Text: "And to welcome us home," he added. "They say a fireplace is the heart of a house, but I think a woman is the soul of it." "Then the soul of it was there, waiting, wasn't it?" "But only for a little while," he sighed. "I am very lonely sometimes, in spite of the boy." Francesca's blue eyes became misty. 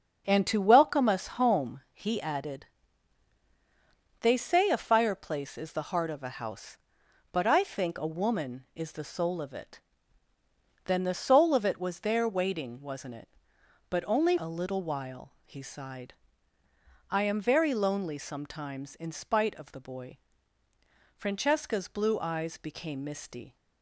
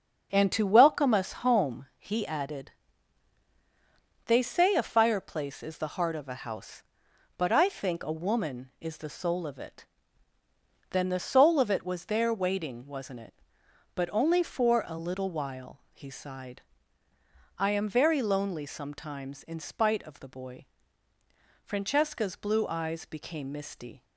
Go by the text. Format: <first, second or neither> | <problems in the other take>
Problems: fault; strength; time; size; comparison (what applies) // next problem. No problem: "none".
second | starts louder than the rest; until 1.2 s; 6.5 dB; also in the second // skips "for"; at 14.3 s